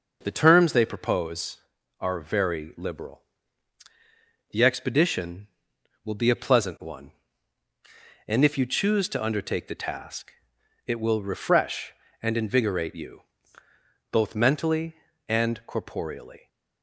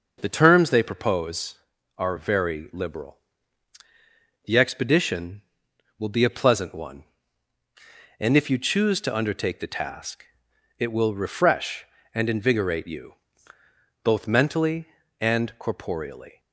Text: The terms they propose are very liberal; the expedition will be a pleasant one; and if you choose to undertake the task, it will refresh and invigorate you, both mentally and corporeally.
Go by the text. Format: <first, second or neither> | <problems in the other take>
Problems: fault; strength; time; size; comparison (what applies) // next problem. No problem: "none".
neither | none